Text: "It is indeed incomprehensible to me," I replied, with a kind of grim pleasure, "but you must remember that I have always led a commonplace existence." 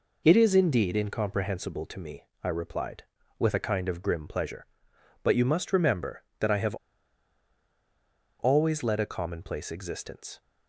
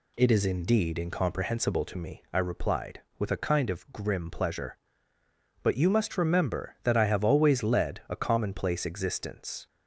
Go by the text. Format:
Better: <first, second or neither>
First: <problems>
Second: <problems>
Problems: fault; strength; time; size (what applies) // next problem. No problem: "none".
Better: second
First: pauses between "have" and "always"; strong; at 6.7 s; 1.6 s long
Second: none